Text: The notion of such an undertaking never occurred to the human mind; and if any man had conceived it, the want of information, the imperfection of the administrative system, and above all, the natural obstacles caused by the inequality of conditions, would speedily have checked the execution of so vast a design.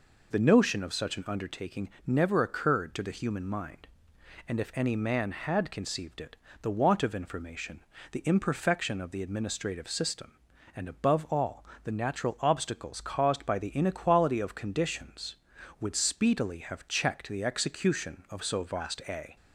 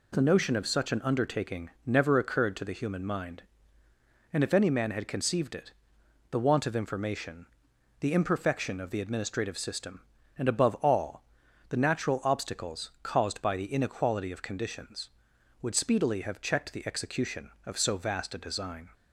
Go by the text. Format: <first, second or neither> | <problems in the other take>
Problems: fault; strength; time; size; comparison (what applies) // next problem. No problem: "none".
second | pauses between "undertaking" and "never"; slight; at 1.8 s; 0.18 s long; slight in the second // stops before "design"; at 19.3 s